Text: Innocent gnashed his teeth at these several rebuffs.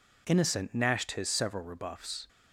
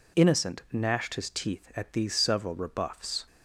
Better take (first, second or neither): second